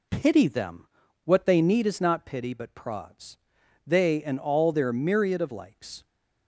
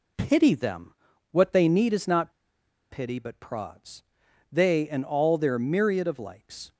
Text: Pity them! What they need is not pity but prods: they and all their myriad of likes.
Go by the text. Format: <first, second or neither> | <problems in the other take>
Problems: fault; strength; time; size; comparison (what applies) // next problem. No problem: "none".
first | pauses between "not" and "pity"; noticeable; at 2.3 s; 0.59 s long